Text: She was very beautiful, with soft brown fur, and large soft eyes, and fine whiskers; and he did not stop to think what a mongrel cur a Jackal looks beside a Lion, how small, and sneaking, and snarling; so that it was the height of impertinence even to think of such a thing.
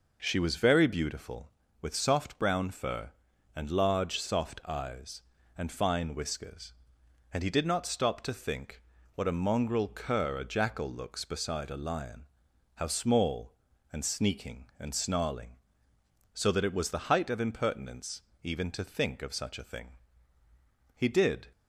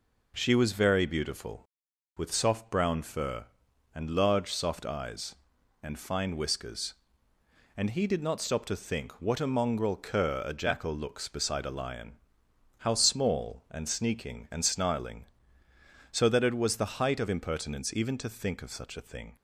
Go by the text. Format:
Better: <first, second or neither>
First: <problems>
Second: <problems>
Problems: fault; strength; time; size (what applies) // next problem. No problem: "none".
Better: second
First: pauses between "think" and "what"; slight; at 8.8 s; 0.32 s long // pauses between "impertinence" and "even"; slight; at 18.2 s; 0.22 s long // goes on to say "He did"; from 20.9 s on; 0.52 s long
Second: none